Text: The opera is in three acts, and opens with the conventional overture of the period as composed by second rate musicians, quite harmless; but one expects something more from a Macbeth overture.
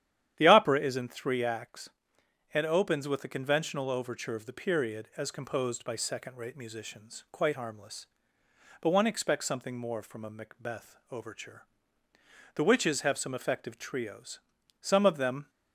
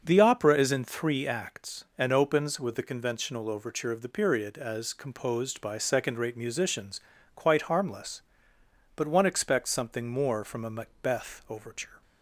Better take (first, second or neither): second